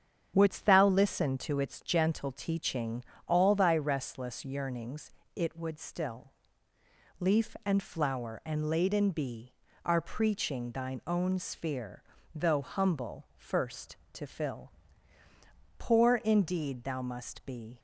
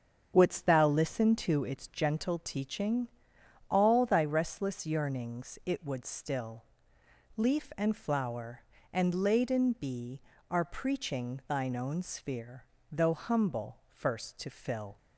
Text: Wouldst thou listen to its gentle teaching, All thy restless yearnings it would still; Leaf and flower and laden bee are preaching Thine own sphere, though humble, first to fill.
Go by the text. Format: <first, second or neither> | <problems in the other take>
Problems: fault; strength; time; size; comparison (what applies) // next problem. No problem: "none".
second | starts louder than the rest; strong; until 1.3 s; 8 dB; strong in the second // pauses between "yearnings" and "it"; slight; at 5.1 s; 0.20 s long // goes on to say "Poor indeed thou must be"; strong; from 15.7 s on; 2.0 s long